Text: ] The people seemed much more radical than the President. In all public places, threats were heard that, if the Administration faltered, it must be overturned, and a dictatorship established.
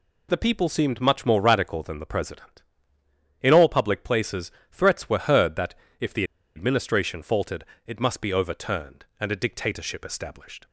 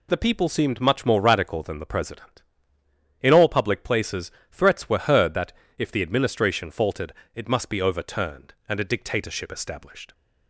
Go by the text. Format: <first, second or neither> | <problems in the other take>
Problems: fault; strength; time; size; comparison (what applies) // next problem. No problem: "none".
second | pauses between "the" and "Administration"; slight; at 6.2 s; 0.32 s long